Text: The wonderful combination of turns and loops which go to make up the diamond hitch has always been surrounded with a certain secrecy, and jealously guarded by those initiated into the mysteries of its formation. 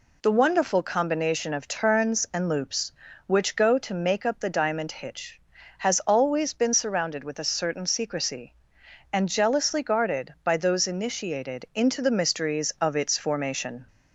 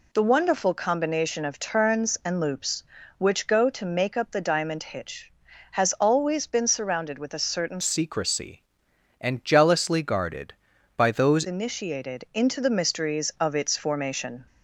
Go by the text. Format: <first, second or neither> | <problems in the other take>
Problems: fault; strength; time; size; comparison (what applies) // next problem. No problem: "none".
first | changes voice from "secrecy" to "those"; from 7.8 to 11.4 s; 3.6 s long